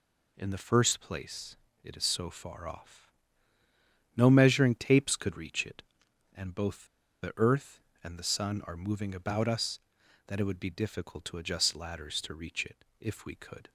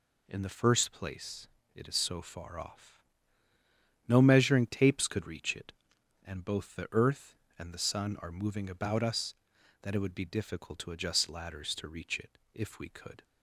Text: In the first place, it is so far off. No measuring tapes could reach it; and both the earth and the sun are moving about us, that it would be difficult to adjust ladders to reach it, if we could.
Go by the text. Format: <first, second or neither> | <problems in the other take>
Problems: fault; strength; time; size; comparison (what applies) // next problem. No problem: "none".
second | pauses between "both" and "the"; slight; at 6.8 s; 0.35 s long